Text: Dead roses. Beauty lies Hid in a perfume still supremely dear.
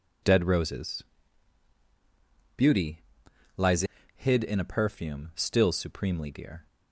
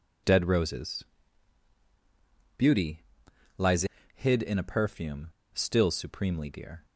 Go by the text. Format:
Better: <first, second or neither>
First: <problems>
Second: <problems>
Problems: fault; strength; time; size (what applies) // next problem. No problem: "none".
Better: first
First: pauses between "Beauty" and "lies"; noticeable; at 2.9 s; 0.56 s long // pauses between "lies" and "Hid"; slight; at 3.8 s; 0.34 s long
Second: pauses between "Beauty" and "lies"; noticeable; at 3.0 s; 0.56 s long // pauses between "lies" and "Hid"; slight; at 3.8 s; 0.32 s long // pauses between "perfume" and "still"; slight; at 5.2 s; 0.26 s long